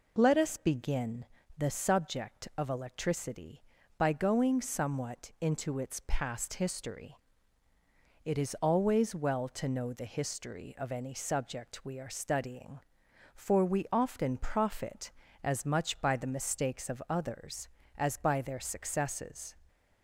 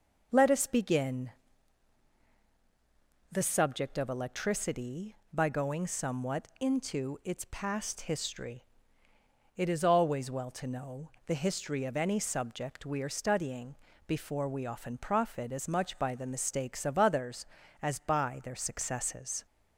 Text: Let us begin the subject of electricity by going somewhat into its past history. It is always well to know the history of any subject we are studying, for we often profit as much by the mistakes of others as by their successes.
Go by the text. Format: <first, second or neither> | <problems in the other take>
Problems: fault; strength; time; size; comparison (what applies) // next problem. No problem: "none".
first | pauses between "begin" and "the"; strong; at 1.2 s; 2.0 s long; slight in the first // pauses between "know" and "the"; slight; at 11.0 s; 0.16 s long // says "before" for "for"; at 14.0 s